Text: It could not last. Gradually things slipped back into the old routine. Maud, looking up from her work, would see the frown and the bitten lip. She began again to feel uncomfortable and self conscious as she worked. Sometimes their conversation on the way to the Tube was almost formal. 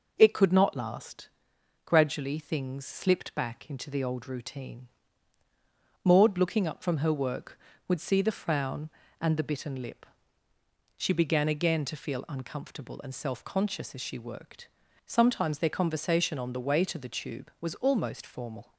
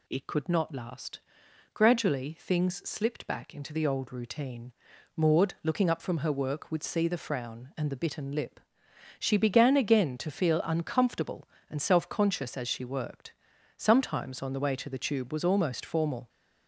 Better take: first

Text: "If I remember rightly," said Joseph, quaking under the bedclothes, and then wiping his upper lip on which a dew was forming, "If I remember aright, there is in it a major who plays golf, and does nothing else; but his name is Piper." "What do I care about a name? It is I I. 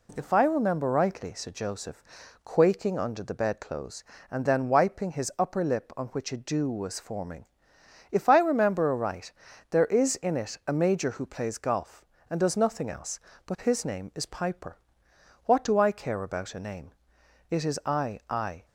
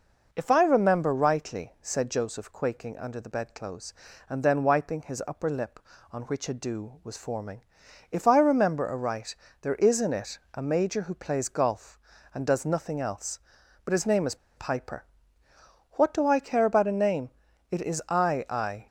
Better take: first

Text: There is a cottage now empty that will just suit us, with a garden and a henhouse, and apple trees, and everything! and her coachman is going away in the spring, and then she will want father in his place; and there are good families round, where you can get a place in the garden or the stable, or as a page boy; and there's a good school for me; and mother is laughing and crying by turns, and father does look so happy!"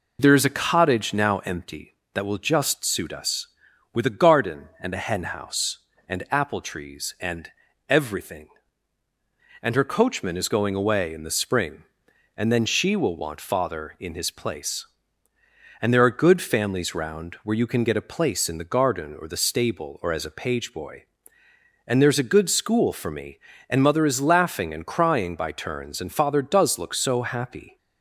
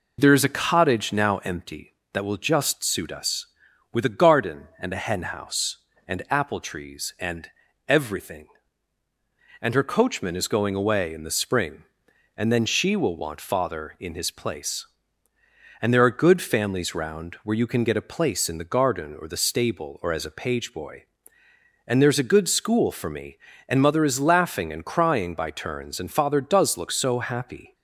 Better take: neither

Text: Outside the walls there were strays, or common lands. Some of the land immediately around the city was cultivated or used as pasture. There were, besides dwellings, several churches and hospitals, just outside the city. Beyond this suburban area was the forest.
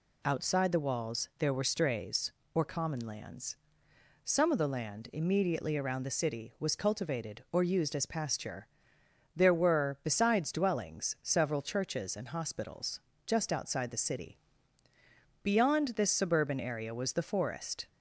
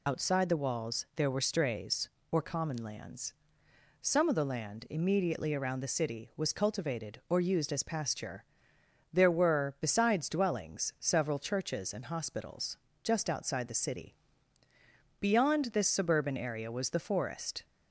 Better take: first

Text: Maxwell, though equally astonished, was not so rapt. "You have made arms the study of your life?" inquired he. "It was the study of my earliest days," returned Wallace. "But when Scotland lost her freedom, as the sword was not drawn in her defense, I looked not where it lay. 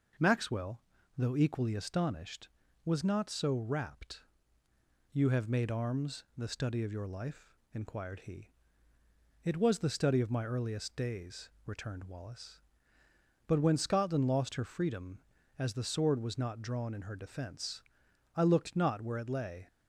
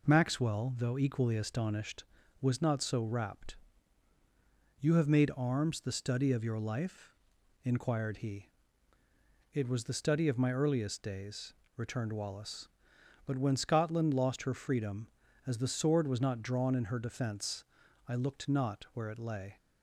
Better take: neither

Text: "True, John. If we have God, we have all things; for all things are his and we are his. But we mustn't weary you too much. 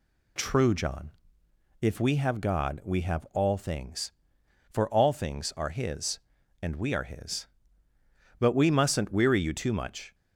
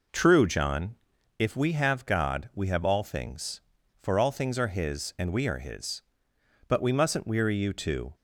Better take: first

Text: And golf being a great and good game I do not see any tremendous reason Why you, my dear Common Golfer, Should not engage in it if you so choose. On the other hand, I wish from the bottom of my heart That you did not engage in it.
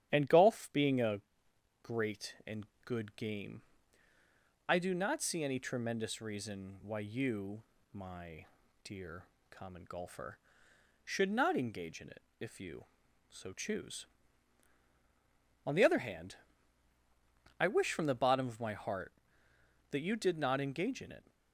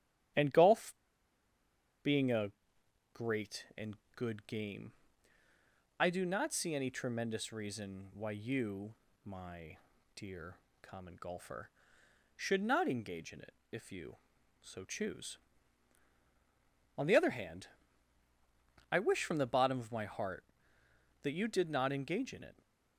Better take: first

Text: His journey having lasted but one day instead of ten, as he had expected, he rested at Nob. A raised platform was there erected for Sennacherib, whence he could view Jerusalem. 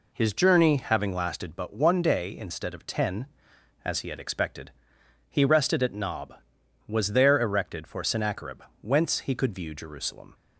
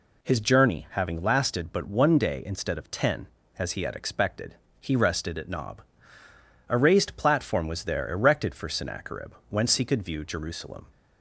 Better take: second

